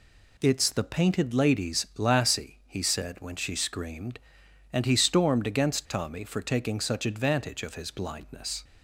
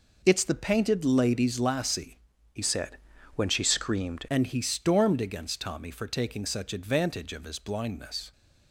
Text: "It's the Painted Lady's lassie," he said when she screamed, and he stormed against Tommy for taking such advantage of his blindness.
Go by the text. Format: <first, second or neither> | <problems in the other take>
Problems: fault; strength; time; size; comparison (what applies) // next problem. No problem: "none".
first | changes voice from "said" to "screamed"; from 2.6 to 4.2 s; 1.6 s long // pauses between "said" and "when"; at 2.9 s; 0.38 s long